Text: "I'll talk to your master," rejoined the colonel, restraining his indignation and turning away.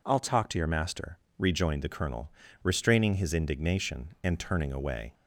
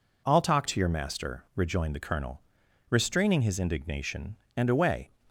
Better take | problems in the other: first | skips "turning"; at 4.6 s

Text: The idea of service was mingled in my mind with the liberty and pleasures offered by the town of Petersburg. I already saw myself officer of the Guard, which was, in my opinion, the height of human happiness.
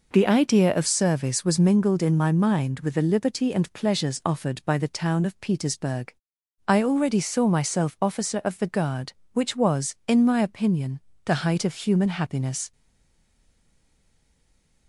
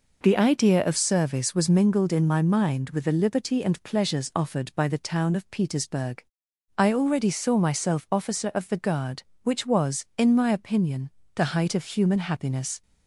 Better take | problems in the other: second | stays silent after the last word; from 12.7 s on; 2.1 s long

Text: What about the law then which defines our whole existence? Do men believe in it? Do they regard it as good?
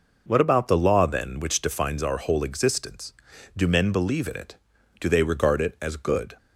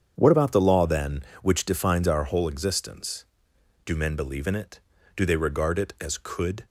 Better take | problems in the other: first | starts louder than the rest; strong; until 1.1 s; 7.5 dB // says "could" for "good"; at 6.1 s

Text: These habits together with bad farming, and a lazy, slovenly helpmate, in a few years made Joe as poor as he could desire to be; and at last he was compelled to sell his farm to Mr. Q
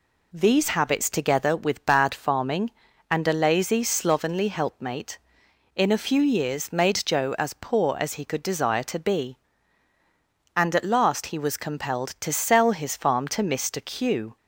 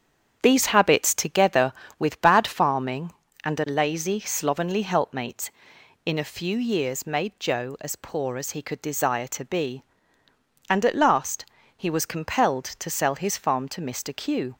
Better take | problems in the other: first | starts louder than the rest; strong; until 1.3 s; 8 dB // pauses between "last" and "he"; slight; at 11.4 s; 0.32 s long

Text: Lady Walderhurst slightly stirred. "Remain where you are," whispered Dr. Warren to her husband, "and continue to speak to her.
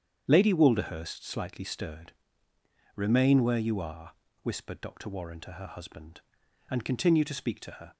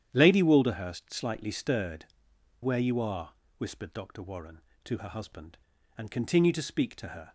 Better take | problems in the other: first | starts louder than the rest; strong; until 1.1 s; 10 dB; strong in the first // skips "Remain"; at 2.3 s

